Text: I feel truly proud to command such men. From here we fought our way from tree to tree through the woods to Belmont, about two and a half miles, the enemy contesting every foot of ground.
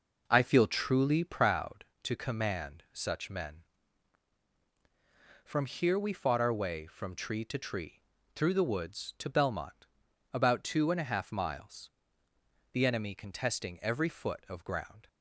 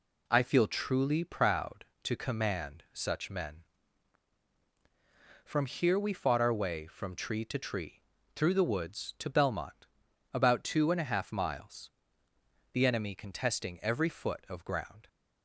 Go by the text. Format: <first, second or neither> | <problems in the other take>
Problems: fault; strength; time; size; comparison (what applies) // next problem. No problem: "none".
second | starts louder than the rest; noticeable; until 1.6 s; 5 dB // pauses between "tree" and "through"; slight; at 8.0 s; 0.32 s long; slight in the second